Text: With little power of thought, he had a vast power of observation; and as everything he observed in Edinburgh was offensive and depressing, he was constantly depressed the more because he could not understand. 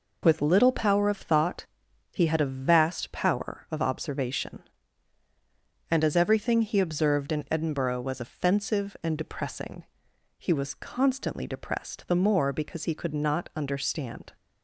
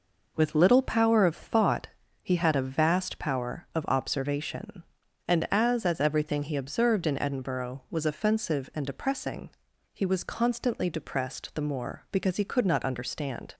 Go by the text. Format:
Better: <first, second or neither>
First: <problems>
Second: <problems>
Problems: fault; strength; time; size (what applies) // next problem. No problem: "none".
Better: first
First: none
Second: says "as" twice; at 5.8 s